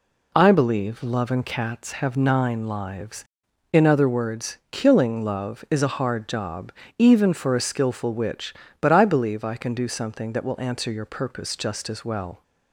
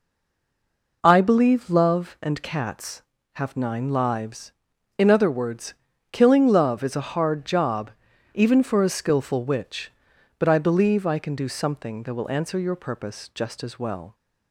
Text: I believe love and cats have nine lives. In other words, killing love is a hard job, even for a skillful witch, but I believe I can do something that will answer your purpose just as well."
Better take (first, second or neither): first